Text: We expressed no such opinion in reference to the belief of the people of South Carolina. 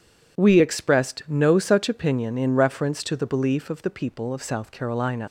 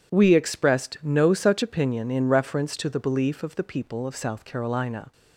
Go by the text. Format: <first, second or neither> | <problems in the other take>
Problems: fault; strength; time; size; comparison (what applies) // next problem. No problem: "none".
second | leaves "Carolina" unfinished; at 5.2 s; 110 ms